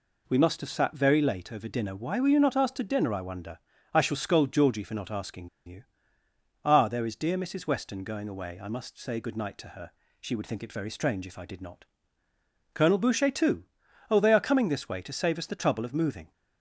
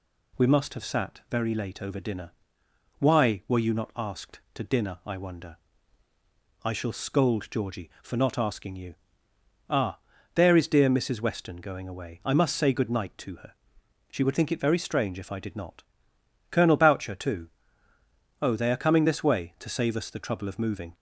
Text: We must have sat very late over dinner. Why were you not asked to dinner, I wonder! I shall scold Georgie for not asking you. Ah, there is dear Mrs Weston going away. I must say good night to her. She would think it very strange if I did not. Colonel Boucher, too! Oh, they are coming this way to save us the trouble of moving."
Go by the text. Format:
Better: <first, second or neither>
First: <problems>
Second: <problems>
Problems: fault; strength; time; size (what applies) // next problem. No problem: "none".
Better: second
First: pauses between "asking" and "you"; slight; at 5.4 s; 0.17 s long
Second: none